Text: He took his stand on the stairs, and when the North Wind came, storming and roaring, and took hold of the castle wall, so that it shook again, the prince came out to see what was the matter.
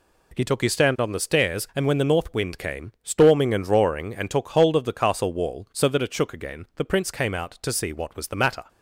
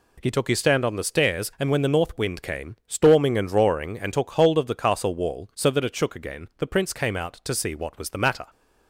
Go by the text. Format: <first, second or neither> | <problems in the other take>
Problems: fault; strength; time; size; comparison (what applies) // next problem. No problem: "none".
neither | none